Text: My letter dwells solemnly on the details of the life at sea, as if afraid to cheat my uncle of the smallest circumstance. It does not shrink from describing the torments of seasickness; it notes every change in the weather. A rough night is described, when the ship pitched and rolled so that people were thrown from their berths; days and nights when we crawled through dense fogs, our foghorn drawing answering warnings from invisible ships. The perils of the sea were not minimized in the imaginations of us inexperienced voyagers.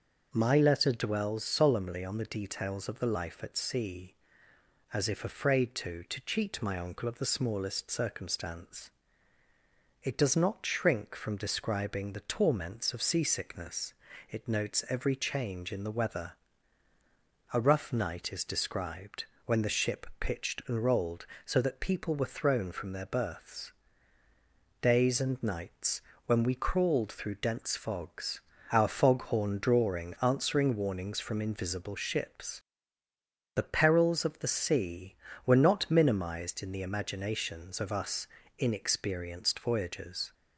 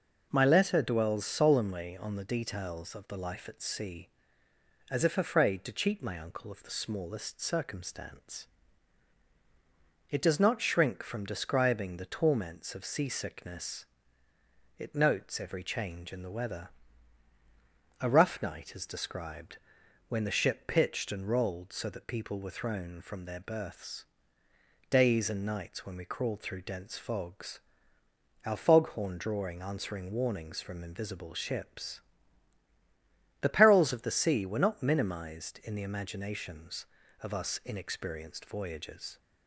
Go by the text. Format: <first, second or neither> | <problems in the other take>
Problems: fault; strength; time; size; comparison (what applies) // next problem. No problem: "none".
second | starts louder than the rest; noticeable; until 1.3 s; 6 dB // says "to" twice; at 6.0 s // pauses between "nights" and "when"; slight; at 26.0 s; 0.24 s long // pauses between "us" and "inexperienced"; slight; at 38.2 s; 0.32 s long